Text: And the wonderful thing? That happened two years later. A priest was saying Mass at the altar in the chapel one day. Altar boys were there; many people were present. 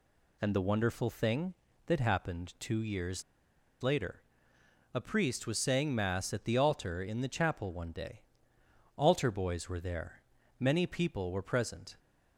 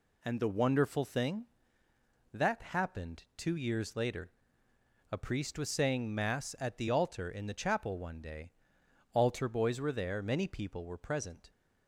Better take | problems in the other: second | pauses between "years" and "later"; noticeable; at 3.2 s; 0.58 s long

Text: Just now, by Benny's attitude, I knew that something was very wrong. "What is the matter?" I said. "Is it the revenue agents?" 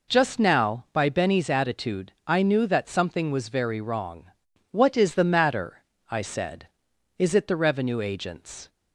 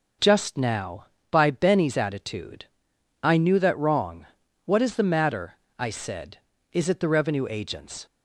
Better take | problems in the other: first | skips "something was very"; at 3.7 s

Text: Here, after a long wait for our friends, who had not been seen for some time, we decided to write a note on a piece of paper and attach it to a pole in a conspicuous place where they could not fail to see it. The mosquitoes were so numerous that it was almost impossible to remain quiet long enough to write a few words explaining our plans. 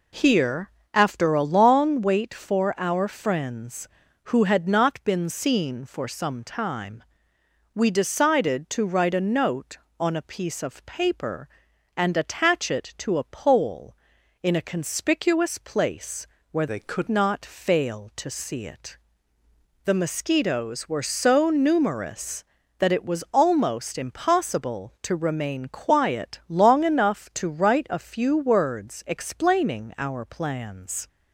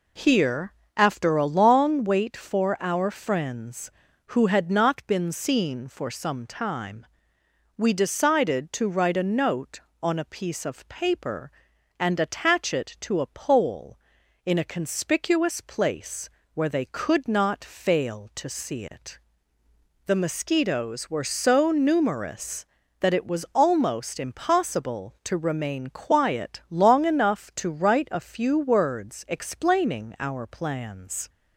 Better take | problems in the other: second | pauses between "place" and "where"; slight; at 16.2 s; 0.24 s long; slight in the second // changes voice from "they" to "could"; from 16.6 to 17.0 s; 0.4 s long

